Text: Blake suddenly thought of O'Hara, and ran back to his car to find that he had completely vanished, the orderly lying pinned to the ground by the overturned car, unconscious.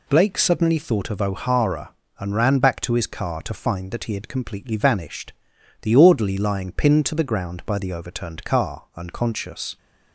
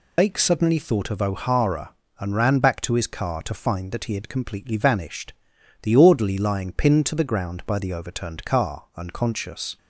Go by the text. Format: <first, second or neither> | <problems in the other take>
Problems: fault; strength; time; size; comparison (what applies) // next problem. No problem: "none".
first | loses the start of "Blake"; at 0.1 s; 90 ms